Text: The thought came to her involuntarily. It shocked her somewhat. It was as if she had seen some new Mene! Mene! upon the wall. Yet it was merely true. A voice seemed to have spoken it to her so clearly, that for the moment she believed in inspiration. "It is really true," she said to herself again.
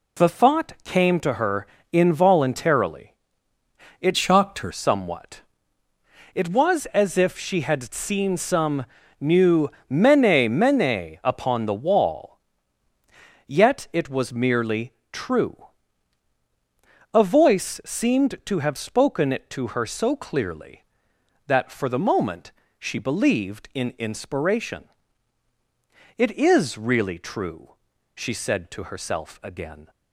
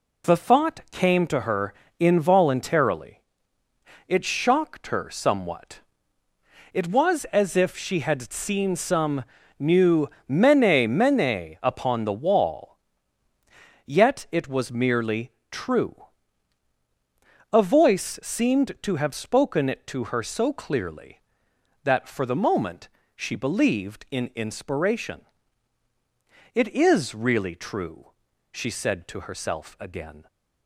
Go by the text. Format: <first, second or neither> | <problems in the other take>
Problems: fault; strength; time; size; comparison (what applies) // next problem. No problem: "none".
second | pauses between "her" and "involuntarily"; slight; at 1.6 s; 0.24 s long; slight in the second // changes voice from "shocked" to "her"; from 4.1 to 4.7 s; 0.6 s long // pauses between "some" and "new"; slight; at 8.8 s; 0.34 s long; slight in the second // pauses between "new" and "Mene"; slight; at 9.6 s; 0.20 s long; slight in the second // pauses between "merely" and "true"; slight; at 14.9 s; 0.20 s long; slight in the second // pauses between "moment" and "she"; slight; at 22.4 s; 0.30 s long; slight in the second